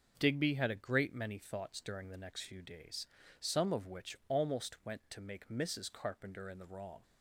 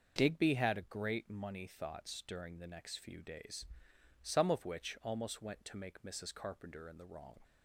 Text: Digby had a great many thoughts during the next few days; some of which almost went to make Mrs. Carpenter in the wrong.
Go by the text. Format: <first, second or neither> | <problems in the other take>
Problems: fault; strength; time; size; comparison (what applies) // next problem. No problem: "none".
first | starts louder than the rest; noticeable; until 1.1 s; 6 dB // says "money" for "many"; at 1.2 s